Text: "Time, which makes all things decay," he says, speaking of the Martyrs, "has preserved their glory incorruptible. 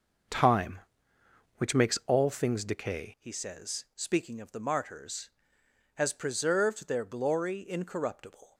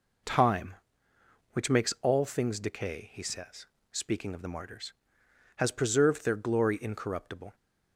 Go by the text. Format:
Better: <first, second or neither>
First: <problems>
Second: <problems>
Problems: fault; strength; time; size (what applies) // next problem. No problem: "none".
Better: second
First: starts louder than the rest; noticeable; until 2.1 s; 6 dB // changes voice at "he"; from 3.1 s on; 5.4 s long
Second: none